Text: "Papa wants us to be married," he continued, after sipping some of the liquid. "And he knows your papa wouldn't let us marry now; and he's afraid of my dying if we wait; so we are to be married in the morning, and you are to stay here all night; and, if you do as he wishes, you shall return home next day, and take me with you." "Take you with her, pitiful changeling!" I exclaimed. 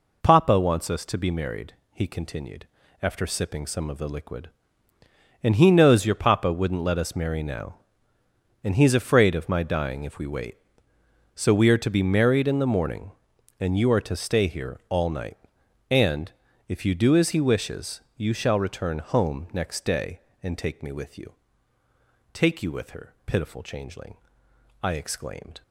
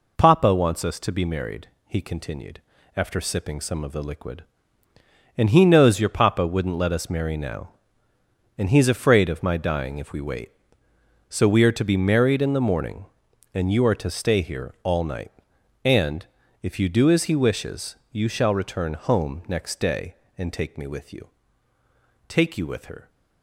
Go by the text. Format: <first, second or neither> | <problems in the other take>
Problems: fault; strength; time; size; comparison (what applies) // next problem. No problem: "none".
first | stops before "pitiful changeling I exclaimed"; at 23.0 s